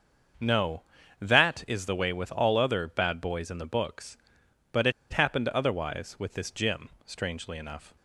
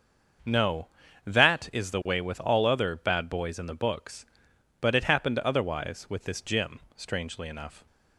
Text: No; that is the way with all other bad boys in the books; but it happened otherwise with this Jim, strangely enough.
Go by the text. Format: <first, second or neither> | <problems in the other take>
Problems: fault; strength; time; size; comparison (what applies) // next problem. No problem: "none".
second | starts louder than the rest; until 1.8 s; 6.5 dB; also in the second // pauses between "it" and "happened"; slight; at 4.9 s; 0.20 s long